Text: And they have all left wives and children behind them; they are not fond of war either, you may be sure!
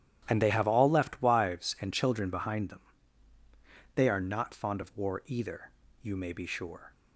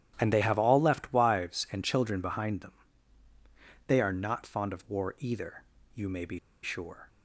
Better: first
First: starts louder than the rest; strong; until 1.2 s; 11.5 dB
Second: starts louder than the rest; strong; until 1.1 s; 11.5 dB // pauses between "be" and "sure"; slight; at 6.3 s; 0.24 s long

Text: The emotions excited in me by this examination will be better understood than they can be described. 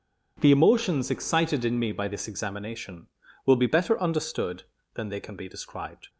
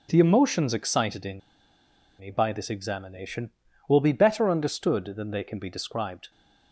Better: first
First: none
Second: starts louder than the rest; noticeable; until 1.1 s; 6 dB // pauses between "in" and "me"; noticeable; at 1.3 s; 0.79 s long

